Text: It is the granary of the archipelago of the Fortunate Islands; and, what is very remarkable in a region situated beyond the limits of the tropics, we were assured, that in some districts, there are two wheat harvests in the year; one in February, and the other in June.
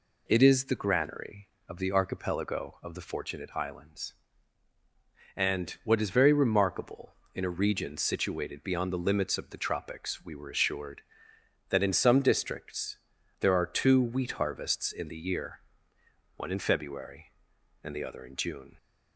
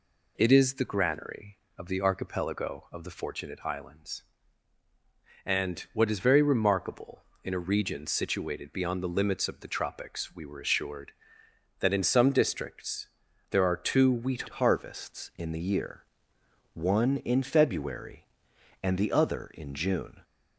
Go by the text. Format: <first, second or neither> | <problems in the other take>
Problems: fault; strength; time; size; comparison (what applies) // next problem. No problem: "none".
first | changes voice at "harvests"; from 14.5 s on; 5.7 s long